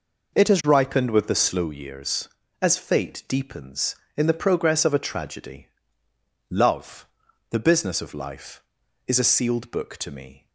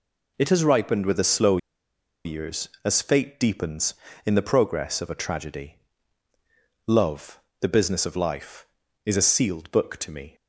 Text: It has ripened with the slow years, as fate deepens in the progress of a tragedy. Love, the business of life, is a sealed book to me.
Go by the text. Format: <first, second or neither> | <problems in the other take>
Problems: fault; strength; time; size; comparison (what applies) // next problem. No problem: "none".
first | pauses between "slow" and "years"; noticeable; at 1.5 s; 0.67 s long